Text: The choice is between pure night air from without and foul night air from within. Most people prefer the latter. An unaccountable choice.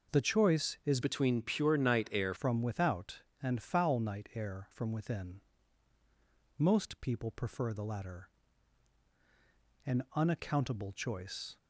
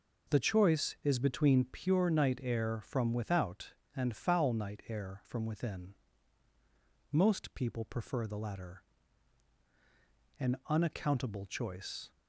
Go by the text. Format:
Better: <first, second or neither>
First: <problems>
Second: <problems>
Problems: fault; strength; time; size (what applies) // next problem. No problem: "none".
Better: second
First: changes voice from "between" to "air"; from 1.0 to 2.3 s; 1.3 s long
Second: none